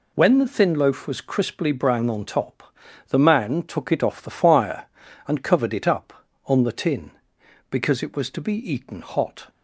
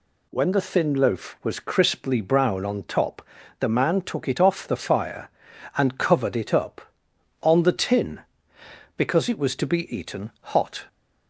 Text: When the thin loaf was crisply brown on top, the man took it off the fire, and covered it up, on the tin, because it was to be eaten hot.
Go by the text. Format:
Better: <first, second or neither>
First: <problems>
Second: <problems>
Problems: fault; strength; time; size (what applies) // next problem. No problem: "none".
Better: neither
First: none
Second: none